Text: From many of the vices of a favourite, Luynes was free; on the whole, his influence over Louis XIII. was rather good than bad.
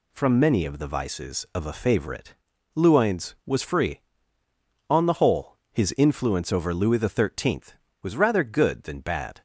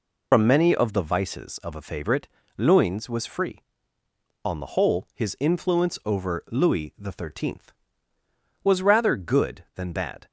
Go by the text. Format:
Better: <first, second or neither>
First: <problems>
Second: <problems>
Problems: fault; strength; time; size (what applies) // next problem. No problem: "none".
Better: first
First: none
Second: loses the start of "From"; at 0.3 s; 70 ms